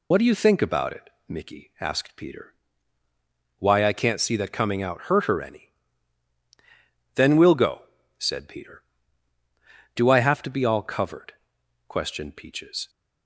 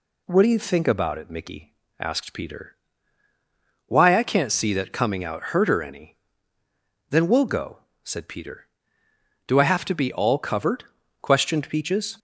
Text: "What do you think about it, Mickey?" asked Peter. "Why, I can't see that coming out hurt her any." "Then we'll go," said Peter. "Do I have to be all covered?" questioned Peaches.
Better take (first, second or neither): second